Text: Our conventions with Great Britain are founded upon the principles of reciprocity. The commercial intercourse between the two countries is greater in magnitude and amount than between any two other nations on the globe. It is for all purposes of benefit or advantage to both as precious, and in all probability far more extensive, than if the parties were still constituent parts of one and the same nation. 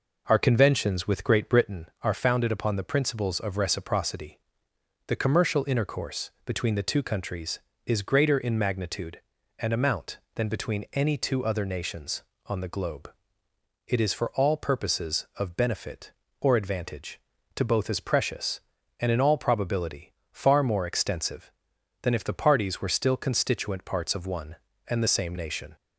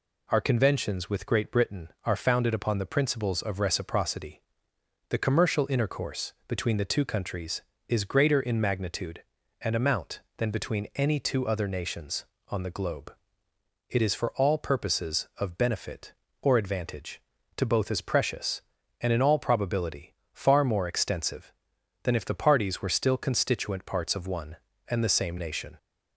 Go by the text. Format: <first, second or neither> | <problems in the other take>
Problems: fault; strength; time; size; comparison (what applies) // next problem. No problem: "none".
second | starts louder than the rest; noticeable; until 1.9 s; 4.5 dB // pauses between "probability" and "far"; slight; at 20.1 s; 0.18 s long; slight in the second